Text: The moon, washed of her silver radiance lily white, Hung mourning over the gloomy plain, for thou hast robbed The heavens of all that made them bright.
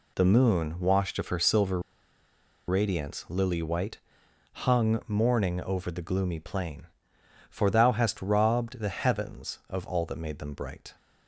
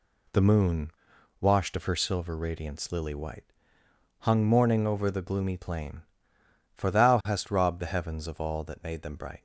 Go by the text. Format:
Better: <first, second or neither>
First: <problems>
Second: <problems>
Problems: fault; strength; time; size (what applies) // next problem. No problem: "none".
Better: second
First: pauses between "silver" and "radiance"; noticeable; at 1.7 s; 0.88 s long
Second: none